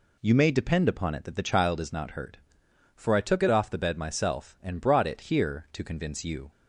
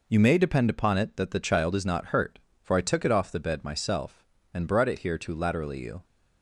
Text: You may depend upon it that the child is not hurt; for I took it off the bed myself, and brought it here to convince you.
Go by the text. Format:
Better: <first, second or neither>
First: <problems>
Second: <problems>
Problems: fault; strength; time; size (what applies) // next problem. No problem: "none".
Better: first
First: none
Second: says "laterally" for "convince"; at 5.3 s